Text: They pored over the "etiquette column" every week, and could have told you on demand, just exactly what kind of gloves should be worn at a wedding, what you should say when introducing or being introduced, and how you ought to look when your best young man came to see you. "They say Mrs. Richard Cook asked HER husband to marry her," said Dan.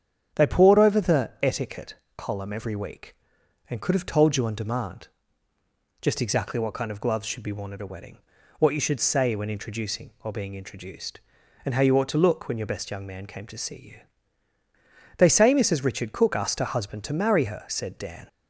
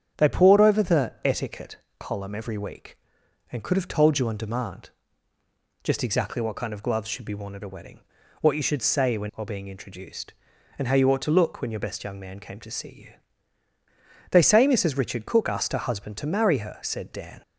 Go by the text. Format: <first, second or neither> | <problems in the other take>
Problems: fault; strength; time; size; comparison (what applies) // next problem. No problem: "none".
first | starts louder than the rest; strong; until 1.2 s; 9 dB; strong in the first // pauses between "etiquette" and "column"; slight; at 1.7 s; 0.22 s long; slight in the first // skips "introducing"; at 9.3 s